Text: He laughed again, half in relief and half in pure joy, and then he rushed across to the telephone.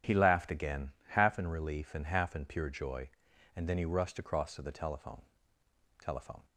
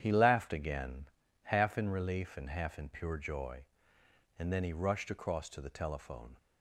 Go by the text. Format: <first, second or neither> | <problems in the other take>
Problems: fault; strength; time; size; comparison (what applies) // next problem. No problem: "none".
second | starts louder than the rest; strong; until 1.2 s; 9 dB; strong in the second // says "telephone" twice; at 5.9 s